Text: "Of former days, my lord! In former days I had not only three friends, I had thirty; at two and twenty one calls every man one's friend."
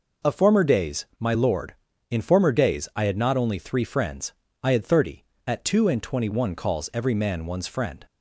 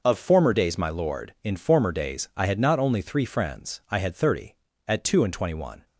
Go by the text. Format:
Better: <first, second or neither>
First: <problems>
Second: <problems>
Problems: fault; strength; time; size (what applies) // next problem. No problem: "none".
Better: first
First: none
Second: stops before "calls every man one's friend"; at 5.8 s